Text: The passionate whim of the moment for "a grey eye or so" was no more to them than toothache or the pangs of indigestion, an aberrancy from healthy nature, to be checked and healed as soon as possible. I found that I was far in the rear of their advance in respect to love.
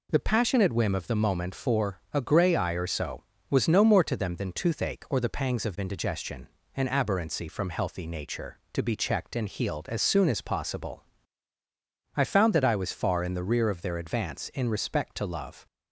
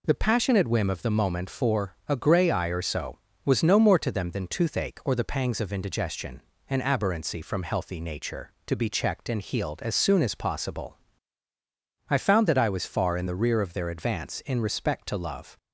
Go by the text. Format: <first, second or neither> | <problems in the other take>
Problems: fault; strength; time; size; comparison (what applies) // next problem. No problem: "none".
neither | none